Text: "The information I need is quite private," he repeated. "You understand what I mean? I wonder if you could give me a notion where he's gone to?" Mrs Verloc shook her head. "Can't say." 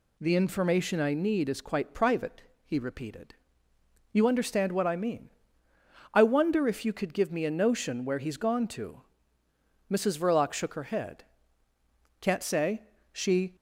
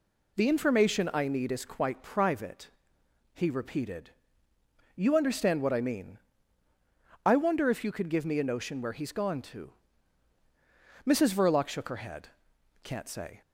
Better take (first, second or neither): second